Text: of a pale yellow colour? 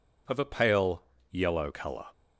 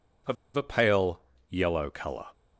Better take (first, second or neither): first